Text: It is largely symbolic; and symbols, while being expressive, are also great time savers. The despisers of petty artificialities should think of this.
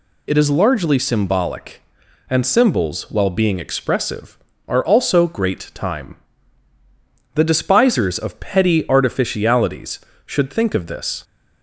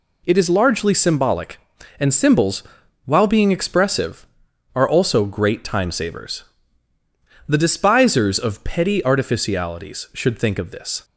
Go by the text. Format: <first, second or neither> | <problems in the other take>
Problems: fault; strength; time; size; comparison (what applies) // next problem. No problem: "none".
second | skips "savers"; at 6.7 s